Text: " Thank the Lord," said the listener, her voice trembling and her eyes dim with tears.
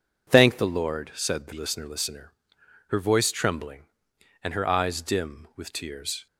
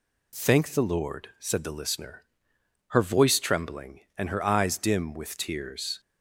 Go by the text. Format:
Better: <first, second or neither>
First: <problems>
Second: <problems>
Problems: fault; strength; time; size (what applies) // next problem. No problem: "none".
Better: second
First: says "listener" twice; at 1.8 s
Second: none